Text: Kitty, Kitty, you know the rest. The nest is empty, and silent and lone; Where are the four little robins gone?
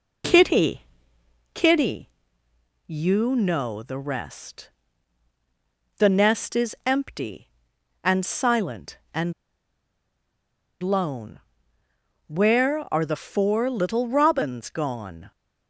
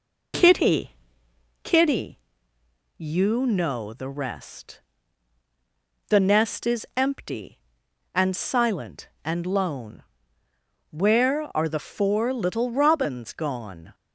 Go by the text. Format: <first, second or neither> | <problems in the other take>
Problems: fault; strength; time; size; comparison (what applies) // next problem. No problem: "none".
second | pauses between "and" and "lone"; strong; at 9.3 s; 1.4 s long